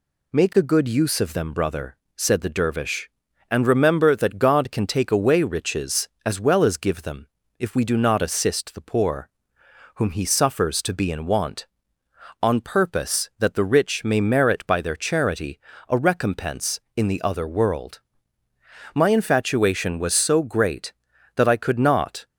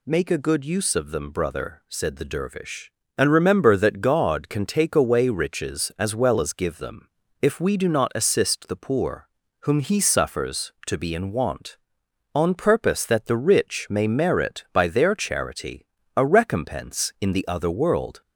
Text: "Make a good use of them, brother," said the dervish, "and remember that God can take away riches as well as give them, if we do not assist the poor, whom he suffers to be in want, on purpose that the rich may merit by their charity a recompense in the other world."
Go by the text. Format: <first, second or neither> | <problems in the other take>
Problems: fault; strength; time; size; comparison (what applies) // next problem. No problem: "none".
second | pauses between "charity" and "a"; slight; at 15.5 s; 0.30 s long; slight in the second // goes on to say "My infatuation was so great that I could not"; strong; from 18.9 s on; 3.3 s long